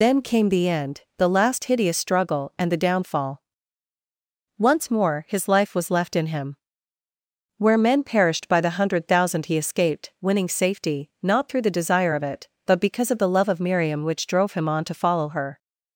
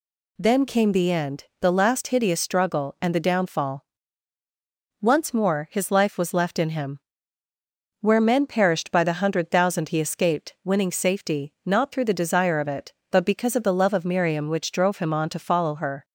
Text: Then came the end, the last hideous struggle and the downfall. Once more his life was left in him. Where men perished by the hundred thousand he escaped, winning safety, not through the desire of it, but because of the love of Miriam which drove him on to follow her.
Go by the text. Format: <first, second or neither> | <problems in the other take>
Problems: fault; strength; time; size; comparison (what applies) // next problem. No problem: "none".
second | loses the start of "Then"; at 0.0 s; 70 ms